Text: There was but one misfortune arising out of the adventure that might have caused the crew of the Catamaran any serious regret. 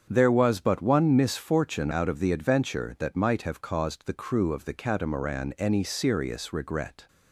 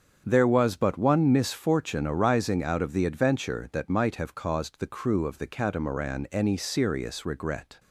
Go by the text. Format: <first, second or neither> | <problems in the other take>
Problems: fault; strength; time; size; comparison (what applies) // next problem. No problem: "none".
second | starts louder than the rest; strong; until 1.1 s; 7.5 dB; strong in the second // skips "arising"; at 1.9 s